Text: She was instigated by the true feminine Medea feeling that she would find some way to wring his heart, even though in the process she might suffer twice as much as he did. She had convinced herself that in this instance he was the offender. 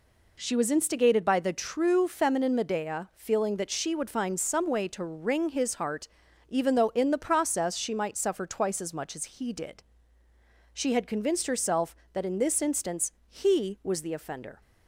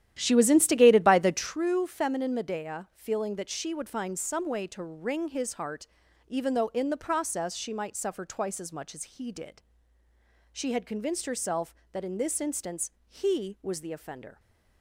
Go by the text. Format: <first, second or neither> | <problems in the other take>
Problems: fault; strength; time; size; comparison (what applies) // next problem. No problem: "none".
first | starts louder than the rest; strong; until 1.7 s; 11.5 dB // pauses between "instance" and "he"; slight; at 12.8 s; 0.18 s long; slight in the first